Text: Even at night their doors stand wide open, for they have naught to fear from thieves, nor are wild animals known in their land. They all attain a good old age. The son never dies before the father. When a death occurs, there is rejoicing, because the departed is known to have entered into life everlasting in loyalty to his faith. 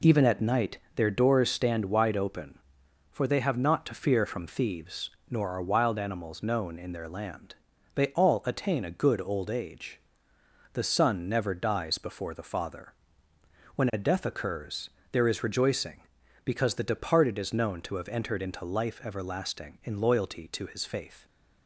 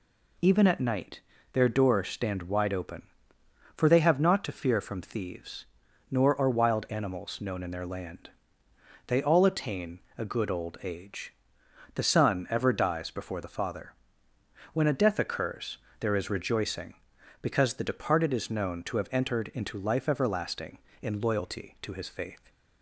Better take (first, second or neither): first